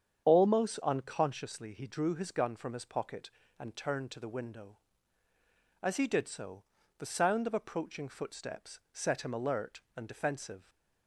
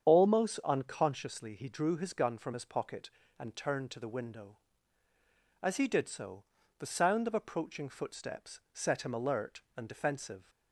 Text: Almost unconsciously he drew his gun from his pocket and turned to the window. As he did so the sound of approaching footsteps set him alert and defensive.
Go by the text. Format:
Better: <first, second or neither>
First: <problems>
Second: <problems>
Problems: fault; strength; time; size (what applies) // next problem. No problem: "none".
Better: neither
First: starts louder than the rest; strong; until 1.3 s; 8 dB // pauses between "so" and "the"; slight; at 6.6 s; 0.36 s long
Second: starts louder than the rest; strong; until 1.1 s; 8 dB // pauses between "so" and "the"; slight; at 6.4 s; 0.36 s long